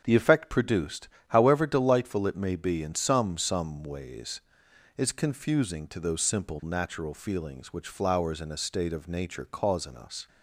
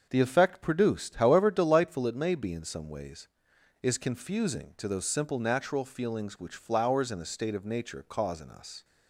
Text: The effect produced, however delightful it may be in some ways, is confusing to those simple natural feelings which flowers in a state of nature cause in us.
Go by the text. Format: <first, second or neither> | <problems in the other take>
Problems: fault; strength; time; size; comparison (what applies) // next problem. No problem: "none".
second | starts louder than the rest; strong; until 1.0 s; 7.5 dB; also in the second // says "some" twice; at 3.3 s